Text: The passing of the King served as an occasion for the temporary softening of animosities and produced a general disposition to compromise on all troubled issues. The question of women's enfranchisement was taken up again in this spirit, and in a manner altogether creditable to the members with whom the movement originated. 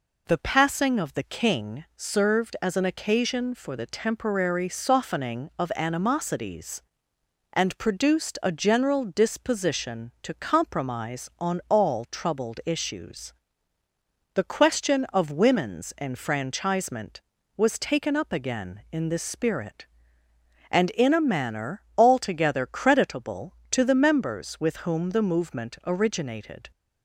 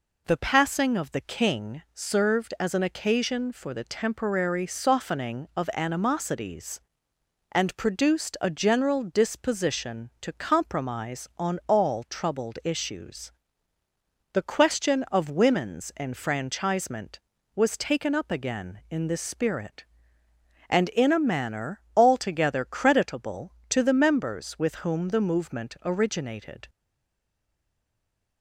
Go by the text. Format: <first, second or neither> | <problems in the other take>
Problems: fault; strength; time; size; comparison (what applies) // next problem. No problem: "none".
first | pauses between "manner" and "altogether"; slight; at 21.8 s; 0.16 s long; slight in the first // stays silent after the last word; noticeable; from 26.6 s on; 1.8 s long